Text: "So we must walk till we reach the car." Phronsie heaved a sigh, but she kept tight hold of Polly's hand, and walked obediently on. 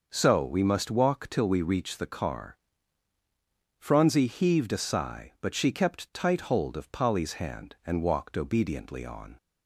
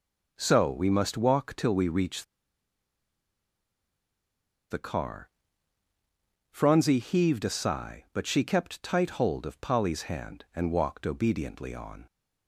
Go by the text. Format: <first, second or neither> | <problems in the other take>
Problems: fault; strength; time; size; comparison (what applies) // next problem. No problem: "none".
first | pauses between "reach" and "the"; strong; at 2.2 s; 2.4 s long